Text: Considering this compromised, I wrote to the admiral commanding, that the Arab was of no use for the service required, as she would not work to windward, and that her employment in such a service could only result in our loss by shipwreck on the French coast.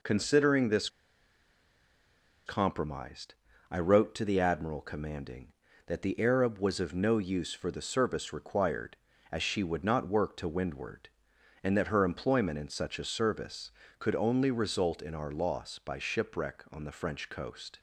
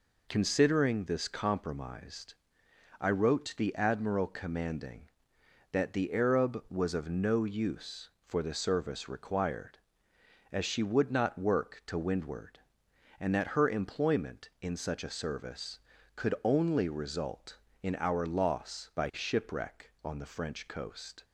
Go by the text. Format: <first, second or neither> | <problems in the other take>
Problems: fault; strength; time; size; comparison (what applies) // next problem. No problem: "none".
second | pauses between "this" and "compromised"; strong; at 0.8 s; 1.5 s long